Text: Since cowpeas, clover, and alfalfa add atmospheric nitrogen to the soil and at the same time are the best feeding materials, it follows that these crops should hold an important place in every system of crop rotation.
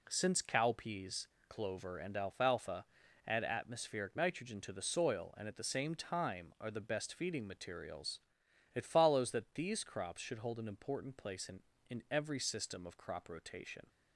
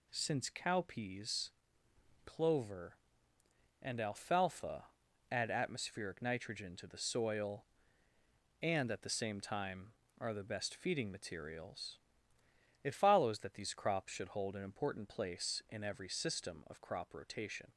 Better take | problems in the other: second | pauses between "alfalfa" and "add"; at 2.8 s; 0.40 s long; noticeable in the second // says "in" twice; at 11.8 s

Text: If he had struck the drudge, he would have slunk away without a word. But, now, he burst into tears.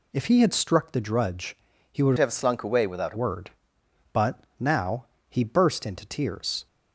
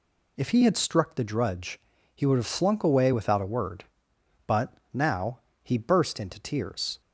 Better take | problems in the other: second | changes voice from "have" to "a"; from 2.1 to 3.1 s; 1.0 s long

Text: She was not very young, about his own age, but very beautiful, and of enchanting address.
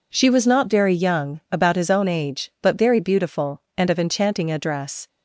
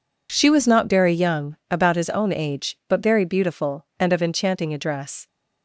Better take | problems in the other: neither | none

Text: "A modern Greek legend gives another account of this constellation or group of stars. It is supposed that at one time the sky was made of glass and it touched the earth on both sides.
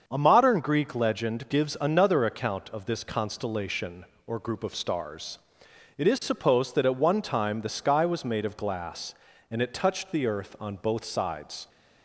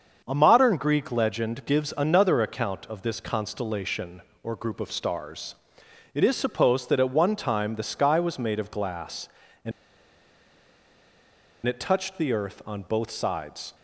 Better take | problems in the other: first | starts louder than the rest; until 1.2 s; 6.5 dB; also in the first // pauses between "and" and "it"; strong; at 9.7 s; 1.9 s long

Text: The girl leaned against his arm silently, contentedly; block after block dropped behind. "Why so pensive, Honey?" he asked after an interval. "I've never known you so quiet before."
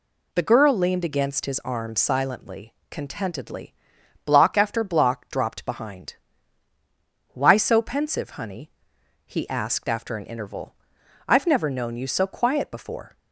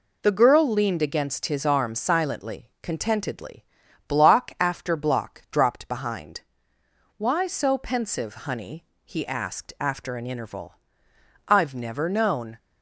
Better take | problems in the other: first | stops before "you so quiet before"; at 12.5 s

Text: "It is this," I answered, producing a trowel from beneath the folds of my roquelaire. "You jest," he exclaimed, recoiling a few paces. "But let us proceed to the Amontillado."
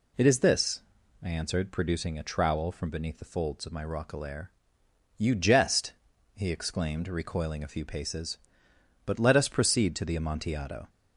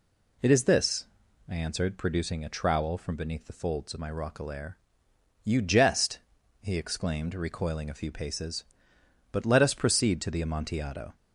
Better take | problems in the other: neither | none

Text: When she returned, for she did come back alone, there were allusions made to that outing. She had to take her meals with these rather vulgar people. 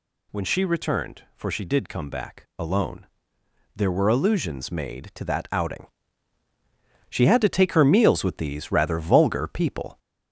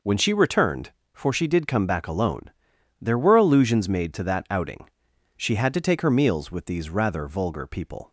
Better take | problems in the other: second | gets louder; slight; throughout; 3 dB

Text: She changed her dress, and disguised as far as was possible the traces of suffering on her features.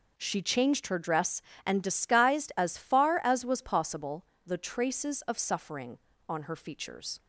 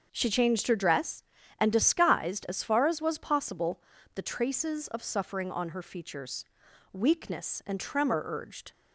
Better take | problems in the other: first | starts louder than the rest; until 1.1 s; 6.5 dB // pauses between "possible" and "the"; slight; at 3.7 s; 0.36 s long; slight in the first // goes on to say "Weakness and tremor urged"; strong; from 6.9 s on; 1.8 s long

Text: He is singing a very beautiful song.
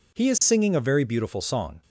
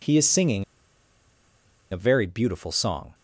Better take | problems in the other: first | pauses between "singing" and "a"; strong; at 0.6 s; 1.2 s long

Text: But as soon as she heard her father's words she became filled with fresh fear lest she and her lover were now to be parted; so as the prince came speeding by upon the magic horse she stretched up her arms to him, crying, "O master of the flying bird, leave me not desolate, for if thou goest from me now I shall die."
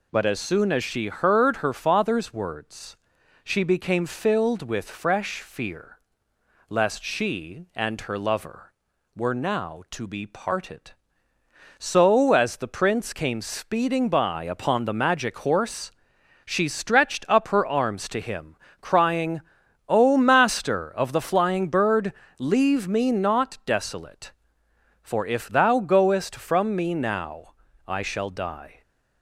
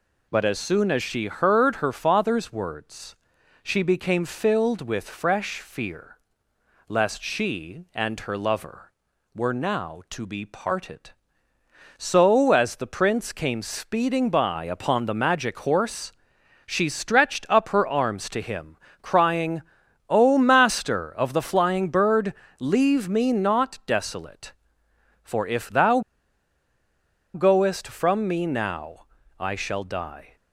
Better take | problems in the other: first | pauses between "words" and "she"; noticeable; at 3.1 s; 0.46 s long; noticeable in the first // pauses between "fear" and "lest"; noticeable; at 6.1 s; 0.70 s long; noticeable in the first // pauses between "horse" and "she"; noticeable; at 16.0 s; 0.56 s long; noticeable in the first // pauses between "thou" and "goest"; strong; at 25.9 s; 1.3 s long // pauses between "now" and "I"; slight; at 29.0 s; 0.32 s long; slight in the first

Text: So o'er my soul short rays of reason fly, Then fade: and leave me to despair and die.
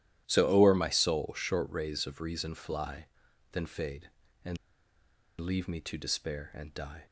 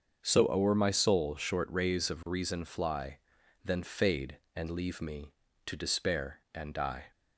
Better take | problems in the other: second | starts louder than the rest; strong; until 1.2 s; 12.5 dB; also in the second // pauses between "and" and "leave"; noticeable; at 4.5 s; 0.82 s long

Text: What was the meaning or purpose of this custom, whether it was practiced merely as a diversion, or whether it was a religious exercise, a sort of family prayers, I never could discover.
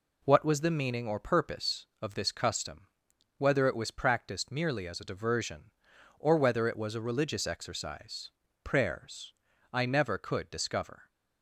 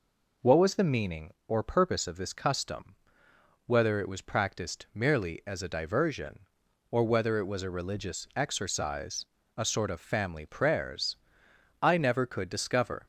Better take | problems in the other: second | skips "a sort of family"; at 8.4 s

